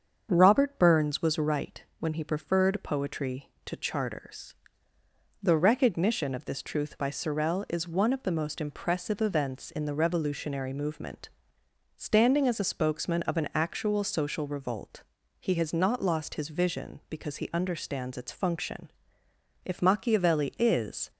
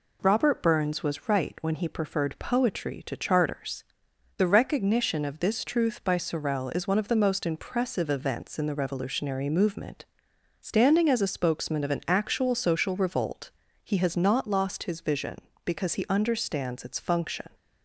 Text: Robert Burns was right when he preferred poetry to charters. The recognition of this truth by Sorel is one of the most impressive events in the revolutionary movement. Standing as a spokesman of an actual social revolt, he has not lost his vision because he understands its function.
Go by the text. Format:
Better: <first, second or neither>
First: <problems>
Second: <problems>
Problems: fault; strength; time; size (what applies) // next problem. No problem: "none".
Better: second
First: starts louder than the rest; strong; until 1.3 s; 7 dB // pauses between "right" and "when"; slight; at 1.8 s; 0.16 s long // goes on to say "If Machiavelli is"; from 19.6 s on; 1.4 s long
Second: none